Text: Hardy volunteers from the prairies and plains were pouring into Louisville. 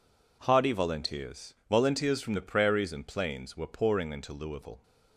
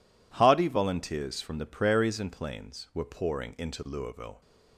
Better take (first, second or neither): second